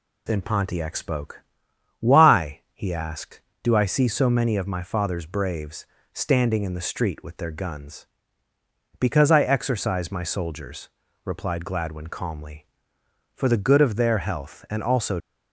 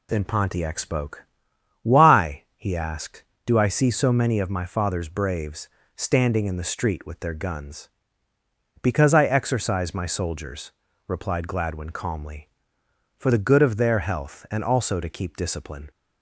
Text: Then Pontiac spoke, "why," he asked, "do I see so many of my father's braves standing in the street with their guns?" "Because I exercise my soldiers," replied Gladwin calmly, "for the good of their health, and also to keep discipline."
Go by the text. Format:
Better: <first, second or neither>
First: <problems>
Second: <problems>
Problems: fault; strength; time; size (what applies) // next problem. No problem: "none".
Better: second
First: pauses between "braves" and "standing"; slight; at 5.8 s; 0.26 s long // stops before "to keep discipline"; at 15.2 s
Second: pauses between "braves" and "standing"; slight; at 5.6 s; 0.26 s long